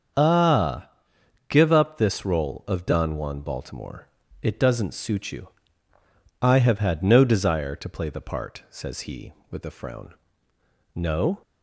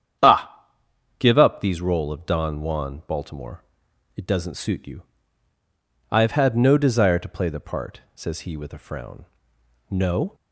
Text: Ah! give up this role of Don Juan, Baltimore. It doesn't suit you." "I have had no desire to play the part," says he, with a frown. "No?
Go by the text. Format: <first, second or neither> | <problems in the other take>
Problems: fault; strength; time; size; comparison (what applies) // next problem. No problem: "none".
first | starts louder than the rest; strong; until 1.7 s; 9 dB; also in the first // says "these" for "this"; at 1.6 s